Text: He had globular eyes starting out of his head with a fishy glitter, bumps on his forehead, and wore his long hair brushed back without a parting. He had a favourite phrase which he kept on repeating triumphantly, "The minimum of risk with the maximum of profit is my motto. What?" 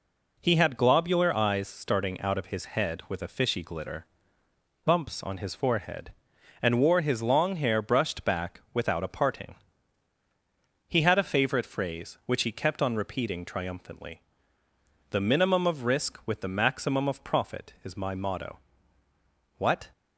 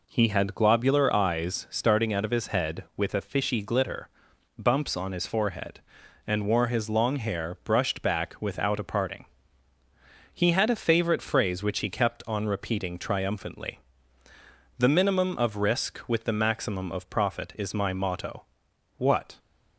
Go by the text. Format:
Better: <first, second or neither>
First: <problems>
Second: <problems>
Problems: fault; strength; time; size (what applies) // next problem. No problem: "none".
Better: neither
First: none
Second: none